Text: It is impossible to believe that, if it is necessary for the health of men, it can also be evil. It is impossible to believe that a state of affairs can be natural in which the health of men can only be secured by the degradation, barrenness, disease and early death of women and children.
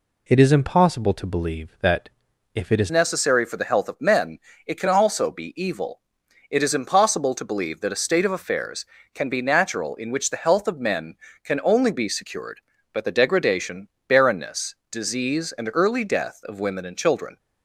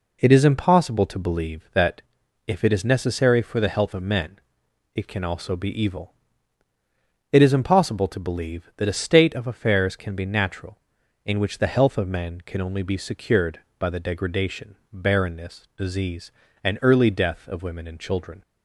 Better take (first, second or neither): second